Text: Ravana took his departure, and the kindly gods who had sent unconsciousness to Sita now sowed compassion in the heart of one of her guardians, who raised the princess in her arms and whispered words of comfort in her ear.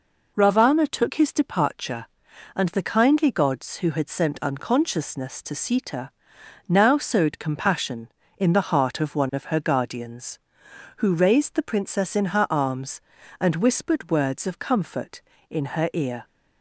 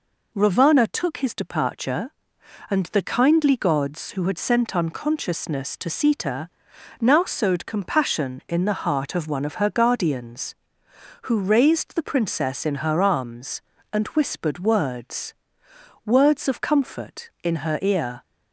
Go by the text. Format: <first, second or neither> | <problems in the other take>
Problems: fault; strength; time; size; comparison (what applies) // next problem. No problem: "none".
first | pauses between "Sita" and "now"; noticeable; at 6.4 s; 0.54 s long; noticeable in the first // says "words" twice; at 16.0 s